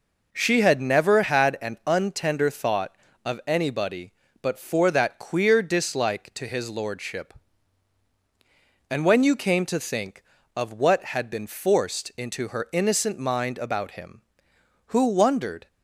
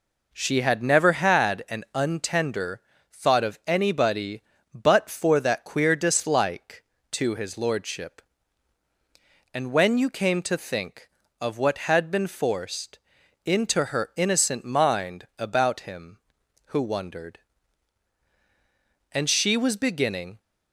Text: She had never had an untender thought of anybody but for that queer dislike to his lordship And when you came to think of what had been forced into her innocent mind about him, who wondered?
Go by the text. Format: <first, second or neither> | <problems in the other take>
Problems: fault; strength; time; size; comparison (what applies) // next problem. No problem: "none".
first | pauses between "untender" and "thought"; slight; at 2.7 s; 0.32 s long // pauses between "forced" and "into"; at 12.9 s; 0.44 s long // goes on to say "And she was beginning"; noticeable; from 19.1 s on; 1.2 s long